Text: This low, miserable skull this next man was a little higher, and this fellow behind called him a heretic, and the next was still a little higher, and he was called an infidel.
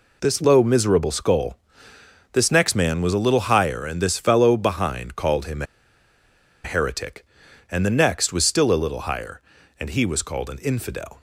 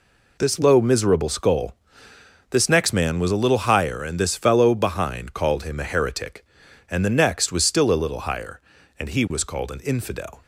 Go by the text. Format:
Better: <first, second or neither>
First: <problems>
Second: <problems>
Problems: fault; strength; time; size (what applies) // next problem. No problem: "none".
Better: second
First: pauses between "skull" and "this"; noticeable; at 1.5 s; 0.76 s long // pauses between "him" and "a"; at 5.6 s; 1.0 s long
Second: pauses between "skull" and "this"; noticeable; at 1.7 s; 0.76 s long